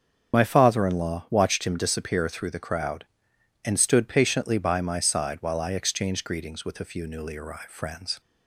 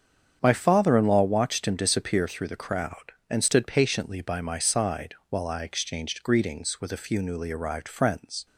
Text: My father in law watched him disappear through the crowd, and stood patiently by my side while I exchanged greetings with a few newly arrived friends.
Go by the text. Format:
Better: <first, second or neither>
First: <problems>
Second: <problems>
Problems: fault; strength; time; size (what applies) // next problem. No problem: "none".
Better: second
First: loses the start of "My"; at 0.3 s; 35 ms // starts louder than the rest; strong; until 1.4 s; 7.5 dB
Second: starts louder than the rest; strong; until 1.4 s; 8 dB